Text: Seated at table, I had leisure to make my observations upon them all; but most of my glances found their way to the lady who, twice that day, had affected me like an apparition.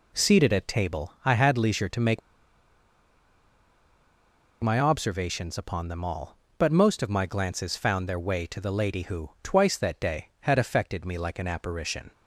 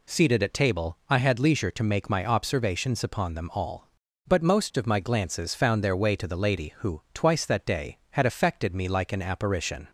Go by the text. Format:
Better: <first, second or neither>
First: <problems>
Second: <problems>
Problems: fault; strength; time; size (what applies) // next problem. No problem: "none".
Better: second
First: pauses between "make" and "my"; strong; at 2.2 s; 2.4 s long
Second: none